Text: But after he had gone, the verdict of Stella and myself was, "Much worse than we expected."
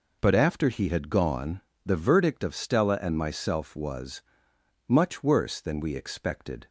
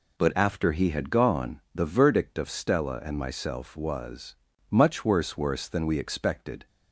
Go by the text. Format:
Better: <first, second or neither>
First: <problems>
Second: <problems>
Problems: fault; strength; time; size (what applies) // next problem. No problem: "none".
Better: first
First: none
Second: says "worse" twice; at 5.3 s